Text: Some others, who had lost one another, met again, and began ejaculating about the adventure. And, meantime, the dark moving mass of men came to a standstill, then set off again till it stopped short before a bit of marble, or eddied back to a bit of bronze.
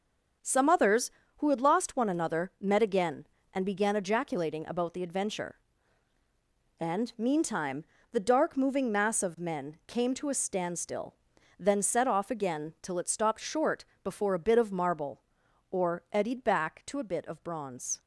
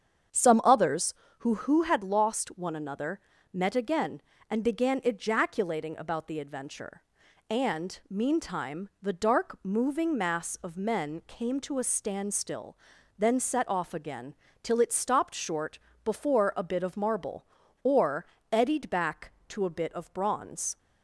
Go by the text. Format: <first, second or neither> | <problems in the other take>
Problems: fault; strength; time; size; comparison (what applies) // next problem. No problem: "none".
first | starts louder than the rest; strong; until 1.6 s; 7.5 dB // says "who" twice; at 1.5 s // pauses between "again" and "till"; slight; at 14.3 s; 0.26 s long // pauses between "short" and "before"; slight; at 15.7 s; 0.26 s long; slight in the first // pauses between "or" and "eddied"; slight; at 18.2 s; 0.28 s long